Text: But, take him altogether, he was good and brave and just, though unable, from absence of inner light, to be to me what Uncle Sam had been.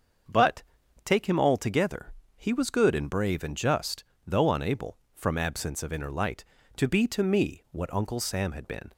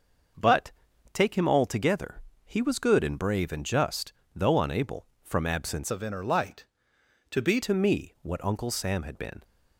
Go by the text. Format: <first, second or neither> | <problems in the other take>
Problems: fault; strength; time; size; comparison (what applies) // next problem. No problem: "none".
first | starts louder than the rest; until 1.7 s; 6 dB; also in the first // changes voice from "of" to "be"; from 5.8 to 7.6 s; 1.8 s long